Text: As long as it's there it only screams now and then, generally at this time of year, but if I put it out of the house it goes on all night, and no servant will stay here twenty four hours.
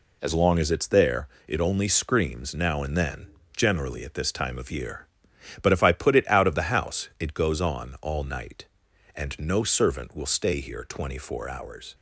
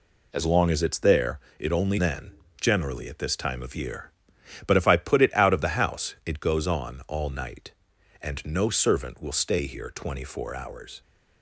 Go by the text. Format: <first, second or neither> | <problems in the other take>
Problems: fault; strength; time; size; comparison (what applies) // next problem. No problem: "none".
first | pauses between "there" and "it"; slight; at 1.3 s; 0.18 s long; slight in the first // skips "screams now and"; at 1.9 s